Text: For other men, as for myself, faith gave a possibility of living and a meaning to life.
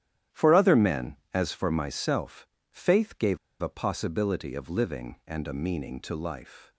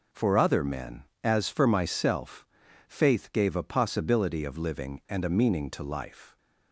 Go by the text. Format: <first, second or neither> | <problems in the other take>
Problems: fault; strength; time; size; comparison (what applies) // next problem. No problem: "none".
second | starts louder than the rest; strong; until 1.4 s; 11.5 dB // pauses between "gave" and "a"; slight; at 3.3 s; 0.24 s long